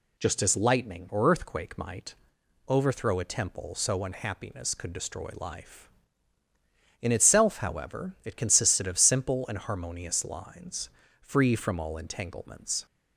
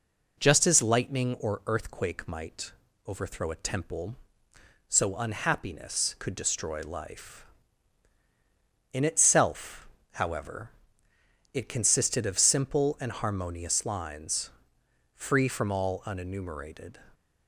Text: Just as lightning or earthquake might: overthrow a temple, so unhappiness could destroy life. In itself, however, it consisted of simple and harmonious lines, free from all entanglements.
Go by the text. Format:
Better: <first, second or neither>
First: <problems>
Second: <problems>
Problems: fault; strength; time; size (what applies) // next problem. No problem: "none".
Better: first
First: none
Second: says "unenumerated" for "entanglements"; at 16.0 s